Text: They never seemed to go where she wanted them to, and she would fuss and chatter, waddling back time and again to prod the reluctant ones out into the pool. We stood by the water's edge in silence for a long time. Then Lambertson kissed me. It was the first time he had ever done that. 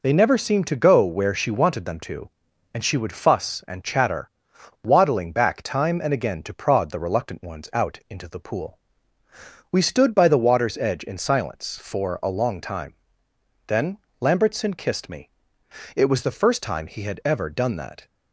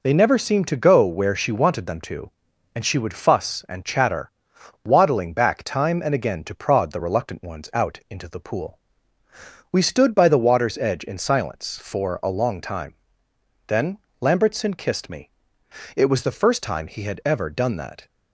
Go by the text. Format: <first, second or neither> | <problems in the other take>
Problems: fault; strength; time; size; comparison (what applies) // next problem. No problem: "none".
neither | pauses between "Then" and "Lambertson"; slight; the same in both